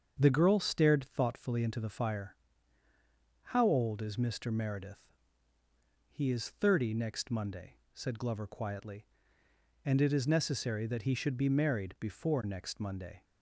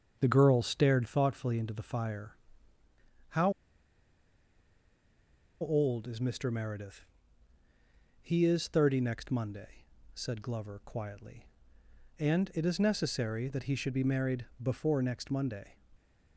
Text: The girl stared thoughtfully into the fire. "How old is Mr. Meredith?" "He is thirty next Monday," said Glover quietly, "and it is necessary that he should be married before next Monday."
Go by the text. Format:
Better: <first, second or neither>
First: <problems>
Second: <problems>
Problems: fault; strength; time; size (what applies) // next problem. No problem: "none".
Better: first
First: starts louder than the rest; until 1.2 s; 7 dB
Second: starts louder than the rest; until 1.2 s; 7 dB // pauses between "How" and "old"; strong; at 3.5 s; 2.1 s long // pauses between "married" and "before"; slight; at 14.4 s; 0.16 s long